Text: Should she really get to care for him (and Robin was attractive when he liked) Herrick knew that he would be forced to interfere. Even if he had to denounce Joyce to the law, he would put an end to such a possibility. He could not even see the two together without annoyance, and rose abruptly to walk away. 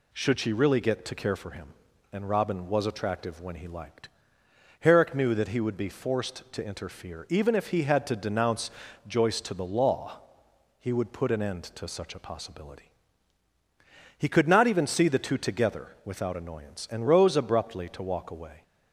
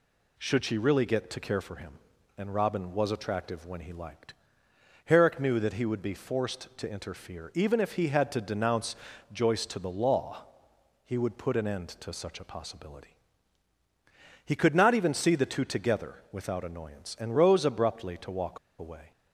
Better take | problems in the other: first | pauses between "denounce" and "Joyce"; slight; at 8.9 s; 0.36 s long; slight in the first // pauses between "walk" and "away"; slight; at 18.5 s; 0.21 s long

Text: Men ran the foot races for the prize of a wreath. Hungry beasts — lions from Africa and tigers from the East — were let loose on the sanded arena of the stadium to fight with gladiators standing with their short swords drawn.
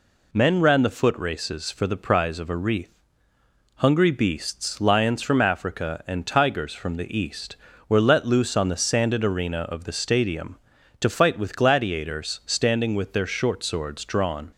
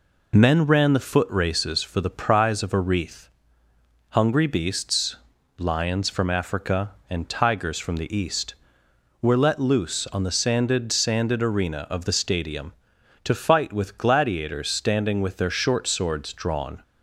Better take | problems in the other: first | says "sanded" twice; at 10.9 s

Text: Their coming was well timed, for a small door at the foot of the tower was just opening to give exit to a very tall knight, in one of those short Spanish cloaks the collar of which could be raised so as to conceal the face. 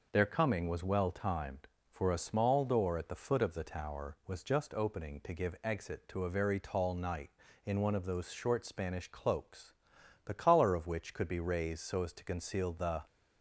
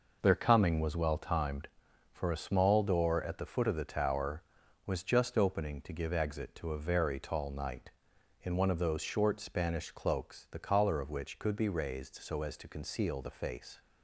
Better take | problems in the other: second | pauses between "cloaks" and "the"; noticeable; at 9.7 s; 0.50 s long // stops before "face"; at 13.0 s

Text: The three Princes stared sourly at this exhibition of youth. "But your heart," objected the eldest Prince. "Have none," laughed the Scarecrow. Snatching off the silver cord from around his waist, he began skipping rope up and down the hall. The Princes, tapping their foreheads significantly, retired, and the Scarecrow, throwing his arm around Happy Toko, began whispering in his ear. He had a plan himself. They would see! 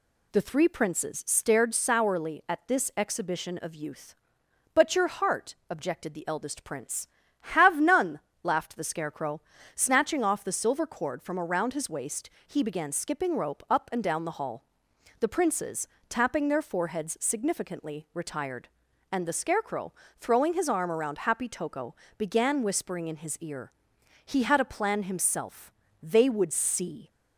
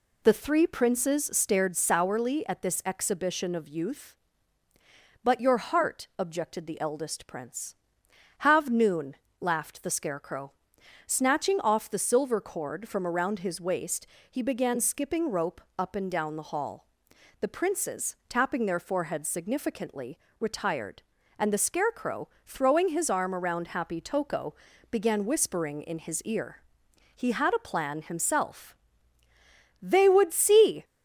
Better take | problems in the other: first | says "noon" for "none"; at 8.7 s // pauses between "rope" and "up"; slight; at 15.6 s; 0.16 s long

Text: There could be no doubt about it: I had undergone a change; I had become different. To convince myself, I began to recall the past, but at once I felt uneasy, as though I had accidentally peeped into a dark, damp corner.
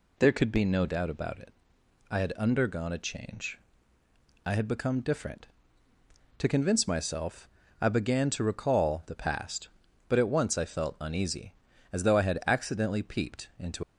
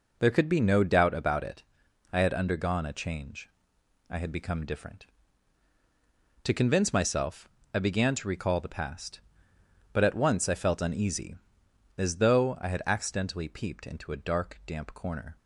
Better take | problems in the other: second | stops before "a dark damp corner"; at 13.8 s

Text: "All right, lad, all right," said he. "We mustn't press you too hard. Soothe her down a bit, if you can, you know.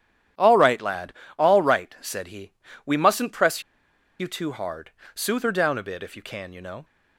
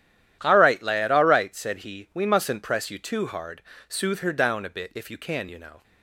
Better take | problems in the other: second | starts louder than the rest; strong; until 1.6 s; 10.5 dB; strong in the second // pauses between "press" and "you"; noticeable; at 3.6 s; 0.58 s long

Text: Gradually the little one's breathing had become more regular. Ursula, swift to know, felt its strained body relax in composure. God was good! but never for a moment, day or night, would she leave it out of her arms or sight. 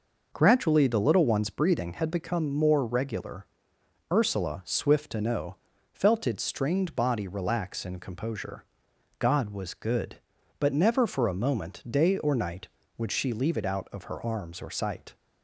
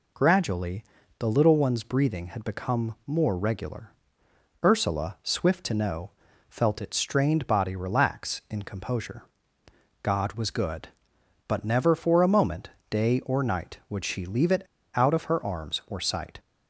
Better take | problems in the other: first | pauses between "Gradually" and "the"; slight; at 0.8 s; 0.34 s long // pauses between "it" and "out"; slight; at 14.6 s; 0.33 s long

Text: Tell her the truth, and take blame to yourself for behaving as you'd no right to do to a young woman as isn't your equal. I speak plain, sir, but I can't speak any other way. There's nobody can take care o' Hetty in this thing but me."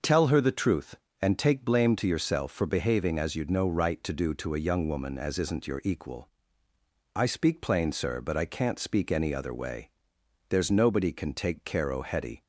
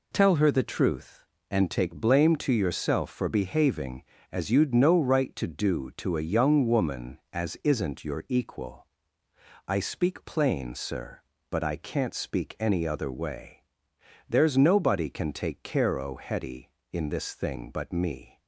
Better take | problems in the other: second | stops before "in this thing but me"; at 12.4 s

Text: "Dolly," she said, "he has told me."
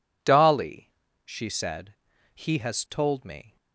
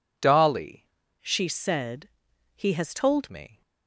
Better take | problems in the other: first | changes voice from "she" to "told"; from 1.2 to 3.2 s; 2.0 s long

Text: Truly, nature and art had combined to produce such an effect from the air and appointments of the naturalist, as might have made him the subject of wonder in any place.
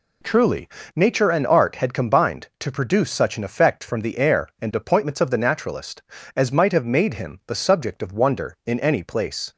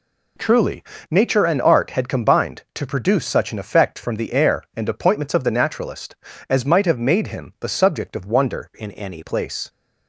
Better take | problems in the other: first | changes voice from "in" to "any"; from 8.7 to 9.2 s; 0.5 s long

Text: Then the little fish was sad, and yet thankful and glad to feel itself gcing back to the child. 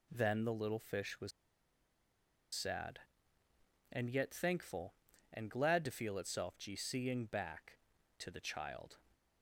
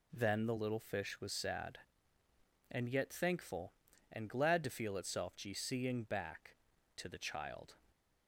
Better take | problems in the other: second | pauses between "was" and "sad"; at 1.3 s; 1.2 s long

